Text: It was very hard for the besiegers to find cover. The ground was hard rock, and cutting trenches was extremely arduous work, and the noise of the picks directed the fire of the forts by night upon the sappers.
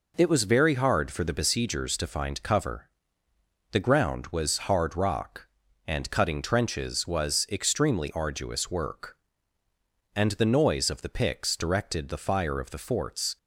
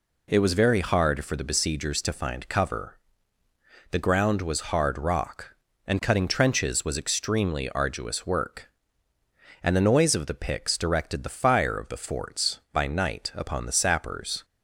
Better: second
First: stops before "by night upon the sappers"; at 13.3 s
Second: none

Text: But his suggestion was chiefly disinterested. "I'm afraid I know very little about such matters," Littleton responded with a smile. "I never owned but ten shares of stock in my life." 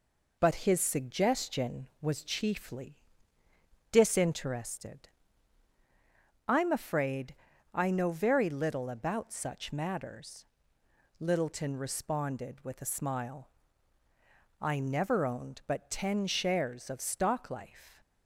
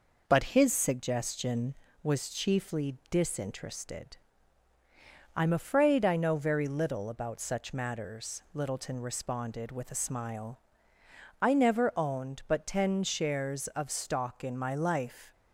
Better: second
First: pauses between "chiefly" and "disinterested"; noticeable; at 3.0 s; 0.88 s long // pauses between "afraid" and "I"; at 7.3 s; 0.40 s long // skips "in my"; at 17.5 s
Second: none

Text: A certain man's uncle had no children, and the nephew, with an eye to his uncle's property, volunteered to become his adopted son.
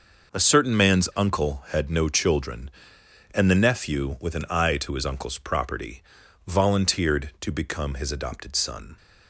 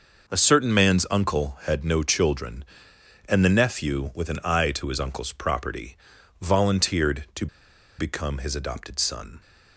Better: first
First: none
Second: pauses between "to" and "become"; noticeable; at 7.4 s; 0.51 s long

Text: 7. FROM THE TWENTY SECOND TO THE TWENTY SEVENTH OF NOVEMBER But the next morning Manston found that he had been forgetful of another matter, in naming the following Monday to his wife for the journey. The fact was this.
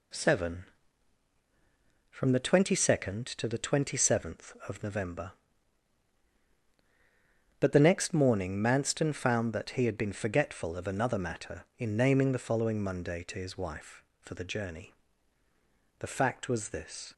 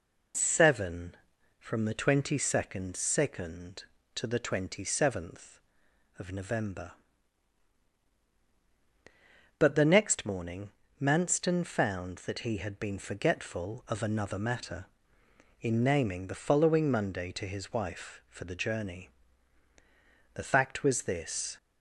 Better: first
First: none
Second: says "SECOND" twice; at 2.9 s // pauses between "morning" and "Manston"; slight; at 10.7 s; 0.28 s long

